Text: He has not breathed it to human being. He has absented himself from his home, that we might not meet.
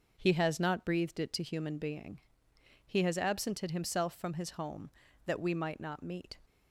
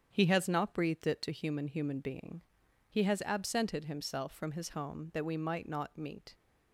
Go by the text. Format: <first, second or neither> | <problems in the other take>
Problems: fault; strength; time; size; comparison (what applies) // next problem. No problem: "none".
first | starts louder than the rest; strong; until 1.1 s; 8 dB // says "human" twice; at 1.6 s